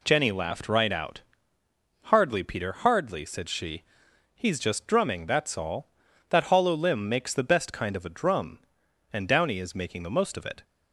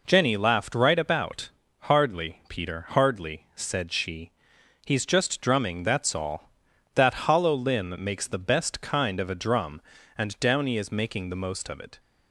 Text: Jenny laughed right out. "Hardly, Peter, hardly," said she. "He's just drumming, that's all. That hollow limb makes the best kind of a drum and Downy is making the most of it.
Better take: first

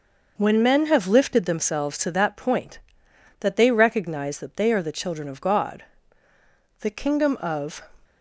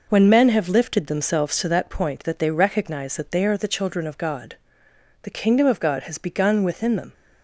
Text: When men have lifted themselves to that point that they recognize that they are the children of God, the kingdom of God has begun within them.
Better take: second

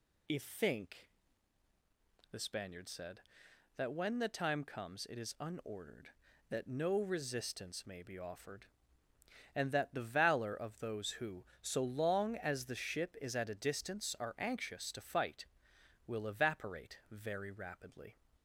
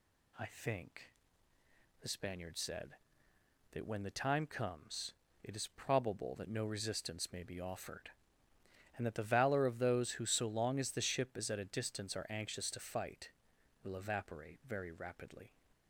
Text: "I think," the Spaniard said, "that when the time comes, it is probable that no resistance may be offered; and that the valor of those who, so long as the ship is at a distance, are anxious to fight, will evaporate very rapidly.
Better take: second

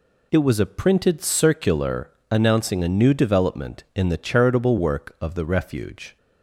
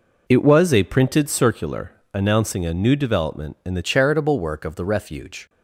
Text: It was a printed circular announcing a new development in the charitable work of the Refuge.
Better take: first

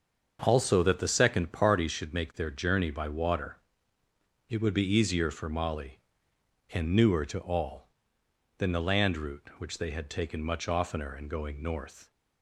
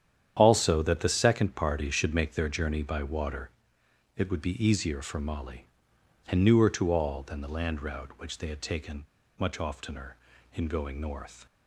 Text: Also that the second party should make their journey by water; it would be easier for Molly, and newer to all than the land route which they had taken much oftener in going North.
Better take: first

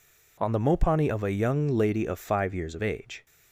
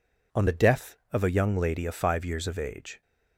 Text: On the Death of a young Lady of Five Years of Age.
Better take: second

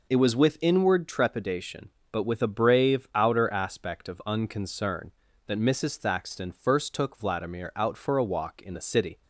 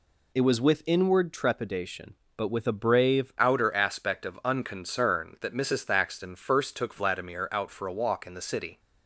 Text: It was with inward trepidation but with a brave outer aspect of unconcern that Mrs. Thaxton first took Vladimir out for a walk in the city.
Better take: first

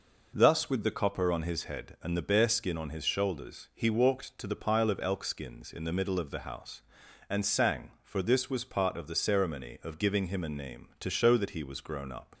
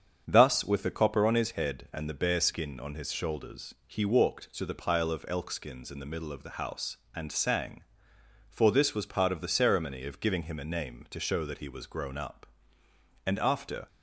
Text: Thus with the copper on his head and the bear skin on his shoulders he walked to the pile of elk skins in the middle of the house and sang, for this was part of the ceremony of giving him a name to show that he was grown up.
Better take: first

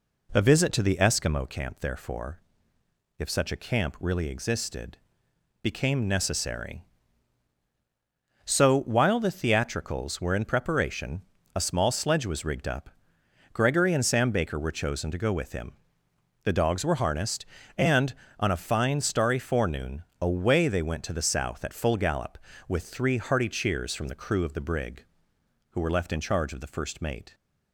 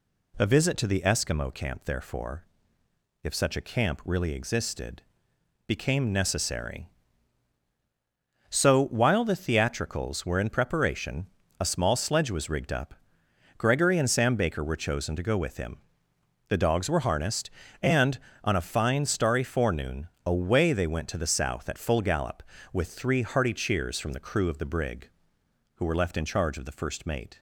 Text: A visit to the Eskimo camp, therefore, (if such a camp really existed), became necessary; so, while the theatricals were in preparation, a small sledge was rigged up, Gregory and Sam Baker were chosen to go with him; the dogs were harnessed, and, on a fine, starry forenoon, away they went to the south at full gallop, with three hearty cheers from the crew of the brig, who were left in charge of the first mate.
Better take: second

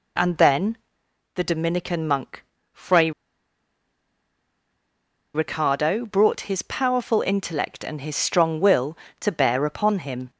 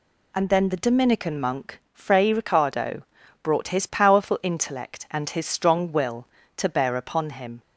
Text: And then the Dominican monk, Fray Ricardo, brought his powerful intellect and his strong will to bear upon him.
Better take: second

